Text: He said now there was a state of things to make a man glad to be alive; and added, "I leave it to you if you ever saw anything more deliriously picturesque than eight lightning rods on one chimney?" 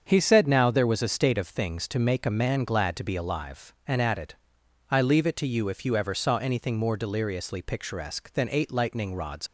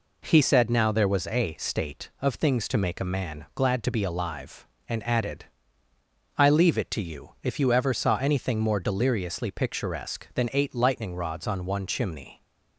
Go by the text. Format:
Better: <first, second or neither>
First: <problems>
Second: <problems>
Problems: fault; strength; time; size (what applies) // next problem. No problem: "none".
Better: second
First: starts louder than the rest; until 1.0 s; 7 dB // stops before "on one chimney"; at 9.4 s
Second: none